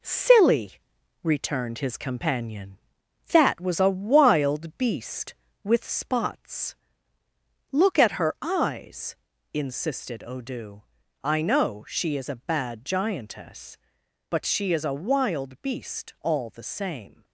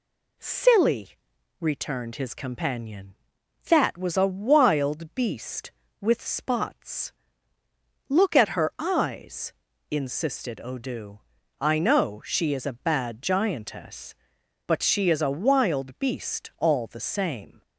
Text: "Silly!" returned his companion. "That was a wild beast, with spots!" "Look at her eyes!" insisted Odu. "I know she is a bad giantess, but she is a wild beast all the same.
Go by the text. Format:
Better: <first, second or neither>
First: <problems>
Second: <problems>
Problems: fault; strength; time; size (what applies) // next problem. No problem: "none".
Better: second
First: gets quieter; noticeable; throughout; 5.5 dB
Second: none